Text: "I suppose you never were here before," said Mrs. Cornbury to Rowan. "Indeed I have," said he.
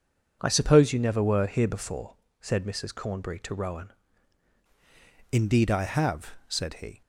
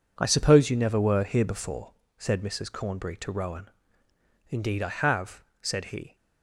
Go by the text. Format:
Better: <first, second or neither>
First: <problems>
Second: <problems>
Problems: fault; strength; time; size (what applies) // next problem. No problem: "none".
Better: second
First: changes voice at "Indeed"; from 5.3 s on; 1.7 s long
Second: none